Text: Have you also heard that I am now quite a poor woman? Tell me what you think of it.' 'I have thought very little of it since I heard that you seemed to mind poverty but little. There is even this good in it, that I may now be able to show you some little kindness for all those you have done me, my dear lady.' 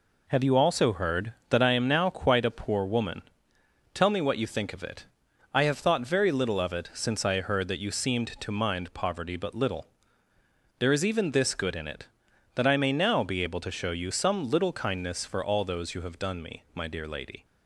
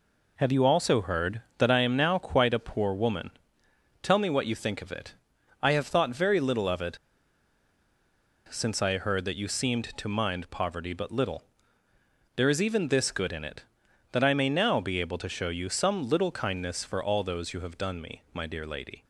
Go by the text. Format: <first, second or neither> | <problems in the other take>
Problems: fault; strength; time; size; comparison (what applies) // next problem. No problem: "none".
first | pauses between "it" and "since"; strong; at 6.9 s; 1.5 s long